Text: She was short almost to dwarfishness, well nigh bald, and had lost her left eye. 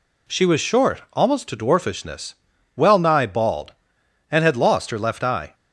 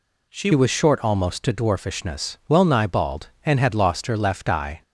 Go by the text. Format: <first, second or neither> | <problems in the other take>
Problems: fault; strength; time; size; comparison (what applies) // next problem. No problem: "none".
first | changes voice at "was"; from 0.5 s on; 4.3 s long